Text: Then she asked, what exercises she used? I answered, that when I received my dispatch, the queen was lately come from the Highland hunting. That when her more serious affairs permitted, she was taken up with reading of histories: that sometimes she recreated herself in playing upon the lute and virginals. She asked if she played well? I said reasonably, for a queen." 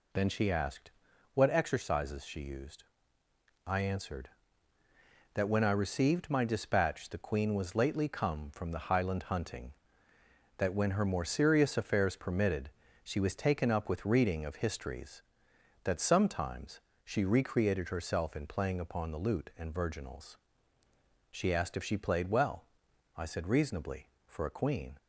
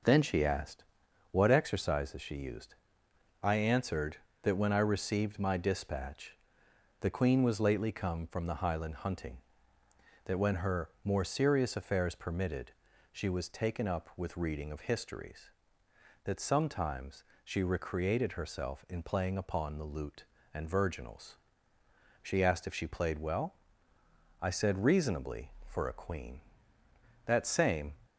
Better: first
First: pauses between "sometimes" and "she"; slight; at 16.7 s; 0.24 s long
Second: pauses between "sometimes" and "she"; slight; at 17.2 s; 0.22 s long // goes on to say "That same"; noticeable; from 27.2 s on; 0.70 s long

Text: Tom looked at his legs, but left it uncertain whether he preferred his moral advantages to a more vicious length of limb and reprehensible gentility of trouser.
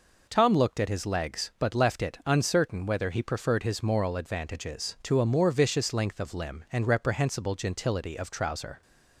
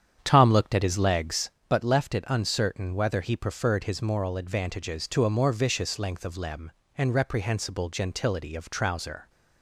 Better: first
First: none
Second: starts louder than the rest; strong; until 1.6 s; 8.5 dB

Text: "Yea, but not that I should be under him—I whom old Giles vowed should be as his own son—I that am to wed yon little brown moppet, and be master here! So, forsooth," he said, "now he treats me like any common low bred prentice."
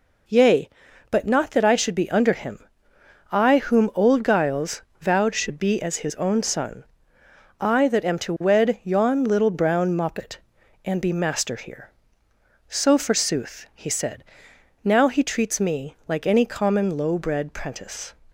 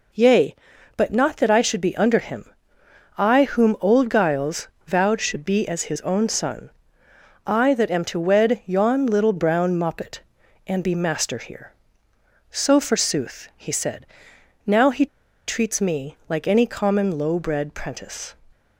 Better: first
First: pauses between "Giles" and "vowed"; slight; at 4.8 s; 0.18 s long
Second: pauses between "Giles" and "vowed"; slight; at 4.6 s; 0.18 s long // pauses between "he" and "treats"; at 15.0 s; 0.41 s long

